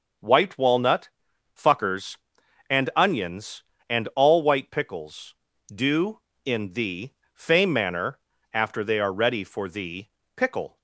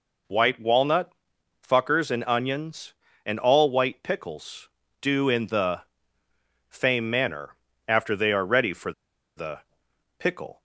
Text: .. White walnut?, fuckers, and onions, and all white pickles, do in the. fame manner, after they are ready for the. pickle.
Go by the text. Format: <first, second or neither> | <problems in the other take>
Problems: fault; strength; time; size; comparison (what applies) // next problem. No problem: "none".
first | pauses between "for" and "the"; noticeable; at 8.9 s; 0.46 s long